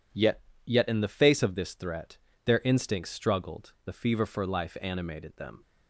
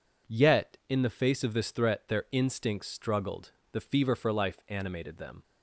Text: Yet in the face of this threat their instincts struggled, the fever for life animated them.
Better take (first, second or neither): second